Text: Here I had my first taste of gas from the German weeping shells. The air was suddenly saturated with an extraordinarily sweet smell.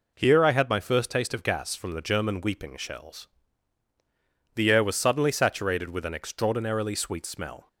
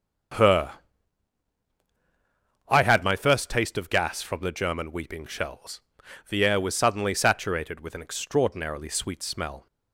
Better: first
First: none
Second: starts louder than the rest; strong; until 3.3 s; 7.5 dB // says "Her" for "Here"; at 0.3 s

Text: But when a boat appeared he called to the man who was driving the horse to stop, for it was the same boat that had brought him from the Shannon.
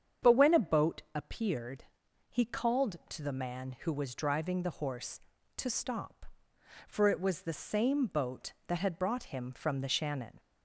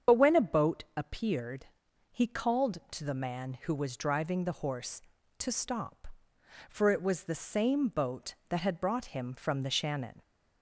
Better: first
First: starts louder than the rest; strong; until 1.3 s; 8 dB // pauses between "appeared" and "he"; noticeable; at 1.8 s; 0.46 s long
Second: loses the start of "But"; at 0.0 s; 35 ms // starts louder than the rest; strong; until 1.2 s; 7.5 dB // pauses between "appeared" and "he"; noticeable; at 1.6 s; 0.46 s long

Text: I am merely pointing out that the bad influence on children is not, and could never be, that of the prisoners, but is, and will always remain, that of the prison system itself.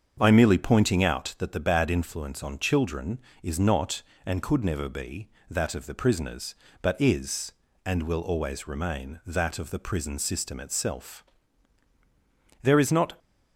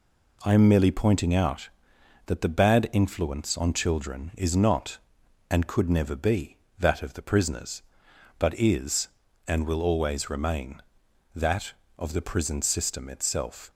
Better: second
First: starts louder than the rest; strong; until 1.2 s; 7 dB // goes on to say "There is not"; from 12.6 s on; 0.56 s long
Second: none

